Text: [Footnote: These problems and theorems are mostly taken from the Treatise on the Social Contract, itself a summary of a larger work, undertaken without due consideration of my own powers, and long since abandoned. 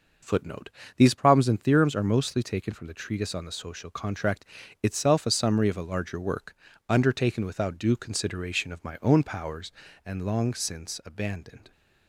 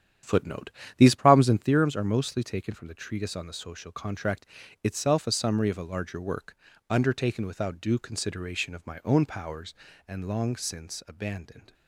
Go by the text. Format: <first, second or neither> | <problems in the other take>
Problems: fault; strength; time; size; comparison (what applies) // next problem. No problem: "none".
first | starts louder than the rest; strong; until 1.7 s; 9.5 dB